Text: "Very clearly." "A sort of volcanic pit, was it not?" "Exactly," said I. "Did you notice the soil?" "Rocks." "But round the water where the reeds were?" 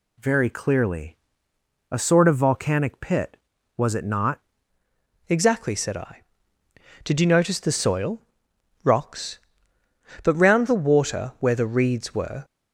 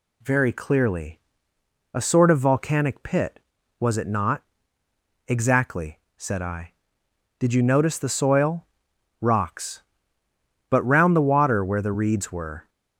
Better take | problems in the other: second | changes voice at "Exactly"; from 5.2 s on; 7.2 s long

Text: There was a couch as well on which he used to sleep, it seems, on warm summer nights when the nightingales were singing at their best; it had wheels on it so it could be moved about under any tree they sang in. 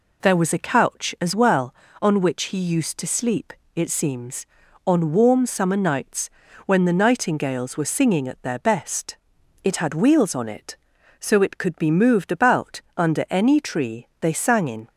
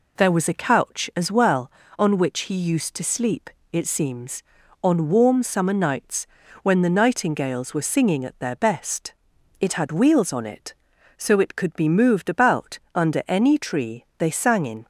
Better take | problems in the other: neither | pauses between "nights" and "when"; slight; the same in both // pauses between "about" and "under"; slight; the same in both

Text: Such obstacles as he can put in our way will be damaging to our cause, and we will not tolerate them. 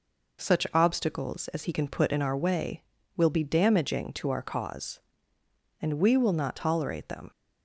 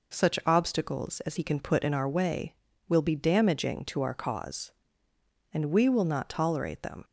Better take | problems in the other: neither | none

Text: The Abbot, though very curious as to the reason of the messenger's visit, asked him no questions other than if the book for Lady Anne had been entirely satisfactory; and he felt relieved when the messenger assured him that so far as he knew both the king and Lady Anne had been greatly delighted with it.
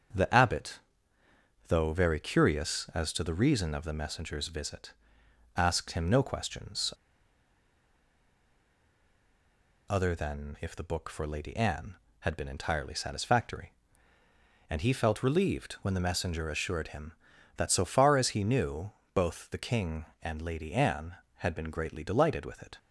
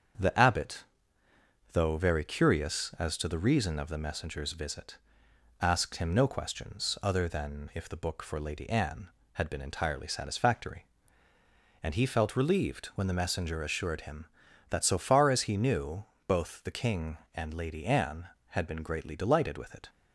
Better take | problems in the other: second | starts louder than the rest; strong; until 2.0 s; 7.5 dB; strong in the second // pauses between "questions" and "other"; strong; at 6.9 s; 2.9 s long // pauses between "knew" and "both"; slight; at 18.9 s; 0.22 s long; slight in the second

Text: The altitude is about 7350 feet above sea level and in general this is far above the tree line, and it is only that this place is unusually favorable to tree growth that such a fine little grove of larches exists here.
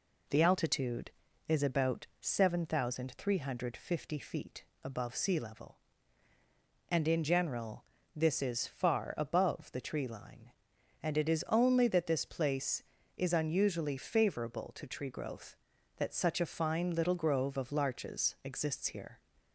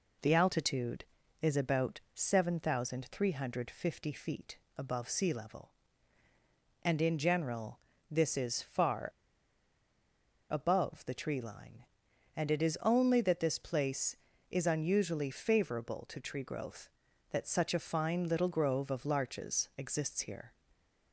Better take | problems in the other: first | pauses between "feet" and "above"; slight; at 4.5 s; 0.20 s long; slight in the first // pauses between "general" and "this"; slight; at 7.7 s; 0.32 s long; slight in the first // pauses between "far" and "above"; strong; at 9.0 s; 1.4 s long

